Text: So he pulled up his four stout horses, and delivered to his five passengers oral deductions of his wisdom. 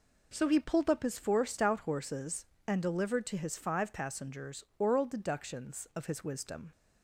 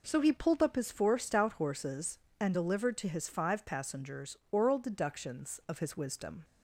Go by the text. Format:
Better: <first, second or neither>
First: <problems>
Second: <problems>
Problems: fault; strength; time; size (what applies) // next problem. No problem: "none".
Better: neither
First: pauses between "passengers" and "oral"; slight; at 4.6 s; 0.16 s long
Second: pauses between "passengers" and "oral"; slight; at 4.3 s; 0.16 s long